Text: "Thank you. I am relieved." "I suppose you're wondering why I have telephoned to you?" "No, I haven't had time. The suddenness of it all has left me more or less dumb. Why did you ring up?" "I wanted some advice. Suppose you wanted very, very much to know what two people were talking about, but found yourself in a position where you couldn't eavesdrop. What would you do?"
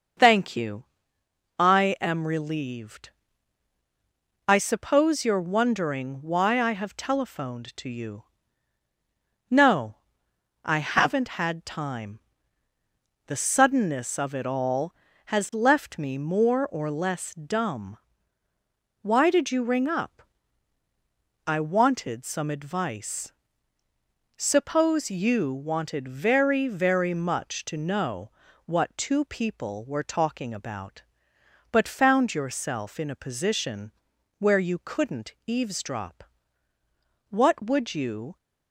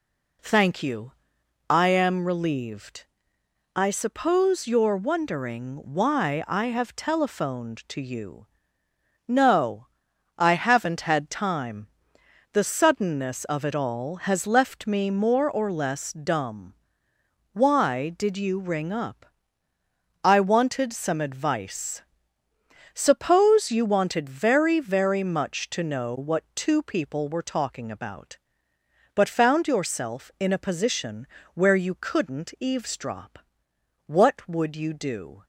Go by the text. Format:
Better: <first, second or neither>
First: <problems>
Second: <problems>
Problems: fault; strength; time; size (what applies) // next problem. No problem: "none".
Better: second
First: starts louder than the rest; until 1.9 s; 6.5 dB // pauses between "know" and "what"; slight; at 28.2 s; 0.36 s long // pauses between "position" and "where"; noticeable; at 33.8 s; 0.48 s long // stops before "do"; at 38.3 s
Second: pauses between "position" and "where"; slight; at 31.2 s; 0.28 s long